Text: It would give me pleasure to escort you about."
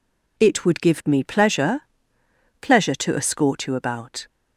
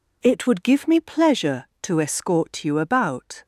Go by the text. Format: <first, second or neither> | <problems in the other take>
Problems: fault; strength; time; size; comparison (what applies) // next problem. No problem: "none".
second | says "pleasure" twice; at 2.5 s